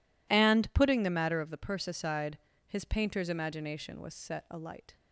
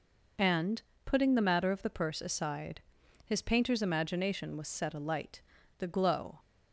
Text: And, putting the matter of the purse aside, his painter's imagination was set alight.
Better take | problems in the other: first | goes on to say "The glow"; from 5.7 s on; 0.60 s long

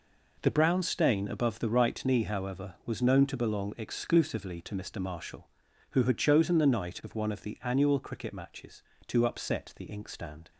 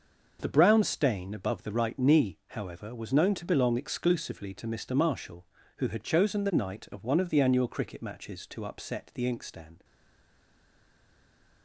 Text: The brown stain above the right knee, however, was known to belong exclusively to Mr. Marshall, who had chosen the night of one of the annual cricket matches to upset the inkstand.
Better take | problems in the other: first | stays silent after the last word; noticeable; from 9.8 s on; 1.8 s long

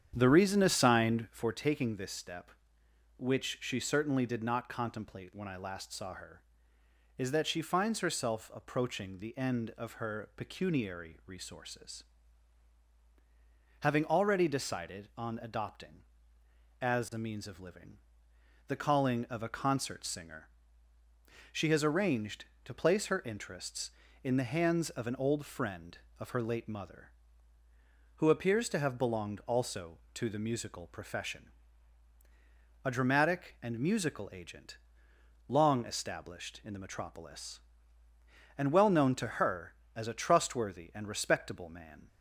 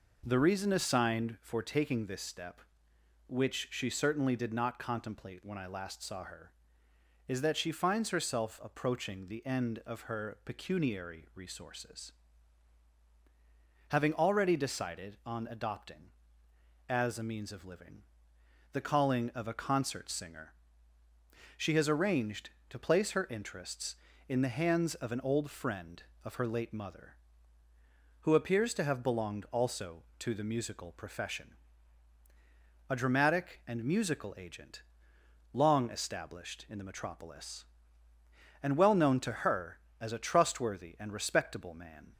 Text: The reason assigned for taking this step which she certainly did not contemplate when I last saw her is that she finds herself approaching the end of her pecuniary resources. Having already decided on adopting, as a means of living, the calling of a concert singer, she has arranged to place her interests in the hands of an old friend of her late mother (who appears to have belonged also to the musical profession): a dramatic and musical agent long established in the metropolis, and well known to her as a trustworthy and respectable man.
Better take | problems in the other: second | starts louder than the rest; strong; until 1.6 s; 9 dB // pauses between "agent" and "long"; noticeable; at 34.7 s; 0.68 s long; noticeable in the second

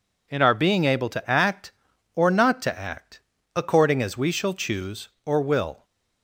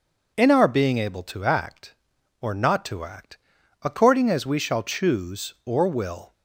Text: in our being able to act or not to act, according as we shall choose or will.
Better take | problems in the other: neither | none

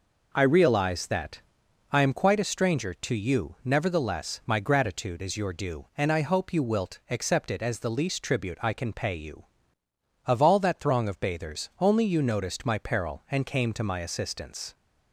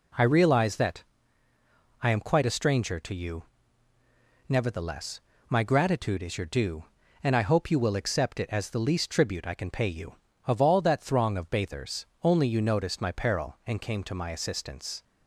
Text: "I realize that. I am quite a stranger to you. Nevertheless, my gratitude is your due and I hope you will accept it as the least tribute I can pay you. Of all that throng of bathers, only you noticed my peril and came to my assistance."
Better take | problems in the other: second | says "wilt" for "will"; at 6.6 s

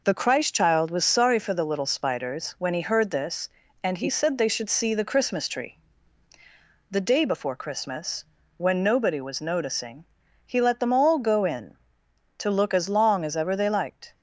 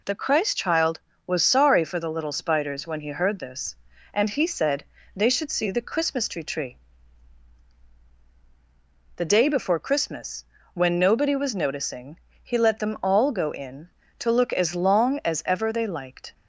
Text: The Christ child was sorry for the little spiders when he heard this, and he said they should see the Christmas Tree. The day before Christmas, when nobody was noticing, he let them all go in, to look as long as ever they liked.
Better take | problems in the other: first | pauses between "said" and "they"; slight; at 4.8 s; 0.32 s long // says "Tree" twice; at 6.4 s

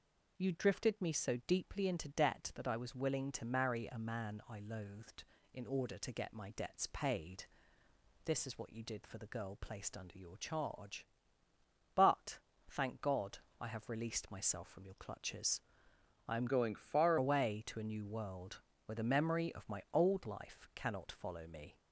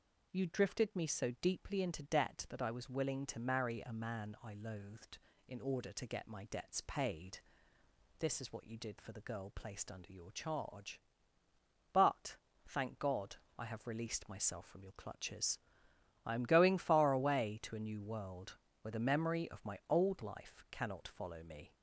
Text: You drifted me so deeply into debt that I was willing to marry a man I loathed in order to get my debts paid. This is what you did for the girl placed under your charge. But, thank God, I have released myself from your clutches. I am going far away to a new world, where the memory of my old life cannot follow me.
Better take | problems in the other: second | changes voice from "going" to "far"; from 16.4 to 17.1 s; 0.7 s long

